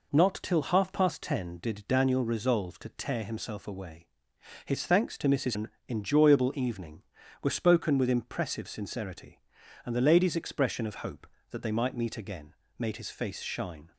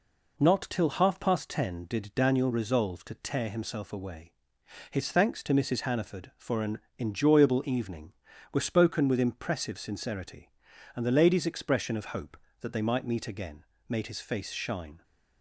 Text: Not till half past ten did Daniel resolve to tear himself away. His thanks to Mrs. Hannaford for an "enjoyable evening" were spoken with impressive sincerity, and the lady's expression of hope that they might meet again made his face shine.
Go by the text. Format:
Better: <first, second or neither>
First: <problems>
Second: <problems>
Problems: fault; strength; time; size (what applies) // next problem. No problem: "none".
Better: second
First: skips "Hannaford for"; at 5.5 s // pauses between "an" and "enjoyable"; slight; at 5.6 s; 0.20 s long // pauses between "again" and "made"; slight; at 12.5 s; 0.24 s long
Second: pauses between "an" and "enjoyable"; slight; at 6.7 s; 0.20 s long // pauses between "again" and "made"; slight; at 13.6 s; 0.24 s long